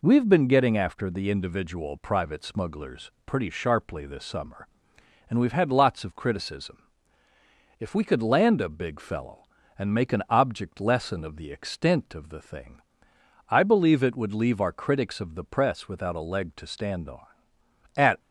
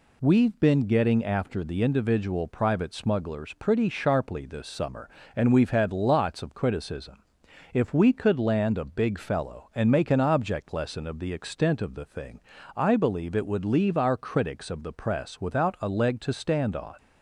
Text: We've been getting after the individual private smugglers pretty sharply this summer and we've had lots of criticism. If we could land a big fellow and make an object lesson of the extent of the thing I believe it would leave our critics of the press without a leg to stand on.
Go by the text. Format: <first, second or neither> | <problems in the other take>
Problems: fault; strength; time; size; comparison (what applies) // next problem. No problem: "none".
second | pauses between "thing" and "I"; noticeable; at 12.8 s; 0.68 s long; slight in the second // goes on to say "At"; slight; from 17.9 s on; 0.24 s long